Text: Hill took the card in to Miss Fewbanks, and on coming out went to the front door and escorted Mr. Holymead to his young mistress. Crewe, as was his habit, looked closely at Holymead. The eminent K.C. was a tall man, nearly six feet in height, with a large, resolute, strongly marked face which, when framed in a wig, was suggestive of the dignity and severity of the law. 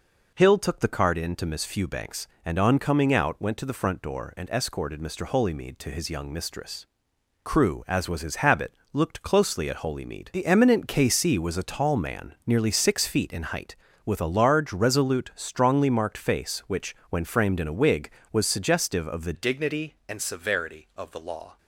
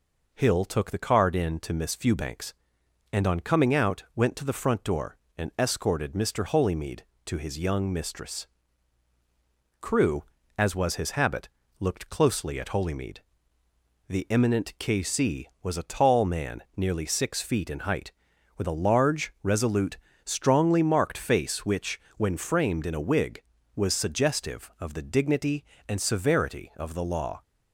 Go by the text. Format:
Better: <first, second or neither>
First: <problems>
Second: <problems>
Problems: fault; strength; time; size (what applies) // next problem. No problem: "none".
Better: second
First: changes voice at "dignity"; from 19.3 s on; 2.2 s long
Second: none